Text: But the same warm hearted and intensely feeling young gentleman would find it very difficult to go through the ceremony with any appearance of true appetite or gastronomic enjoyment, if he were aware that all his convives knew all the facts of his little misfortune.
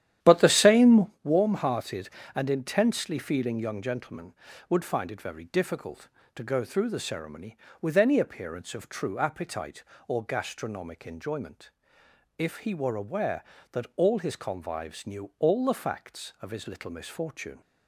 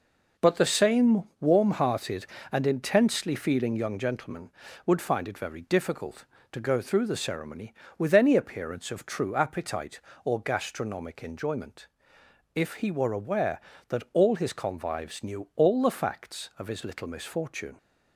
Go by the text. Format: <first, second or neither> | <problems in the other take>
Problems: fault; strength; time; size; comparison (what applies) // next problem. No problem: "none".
second | starts louder than the rest; strong; until 1.2 s; 11 dB // pauses between "same" and "warm"; slight; at 1.0 s; 0.16 s long; slight in the second